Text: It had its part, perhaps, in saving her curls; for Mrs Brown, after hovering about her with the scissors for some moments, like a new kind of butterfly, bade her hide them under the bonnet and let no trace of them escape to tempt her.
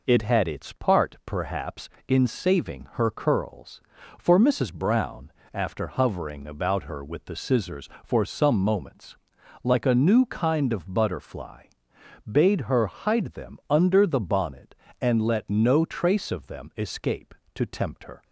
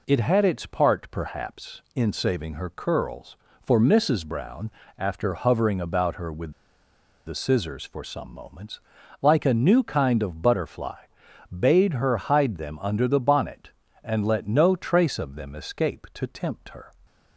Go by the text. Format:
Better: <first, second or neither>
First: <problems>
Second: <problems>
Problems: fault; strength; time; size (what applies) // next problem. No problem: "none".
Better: first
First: none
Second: pauses between "with" and "the"; noticeable; at 6.5 s; 0.74 s long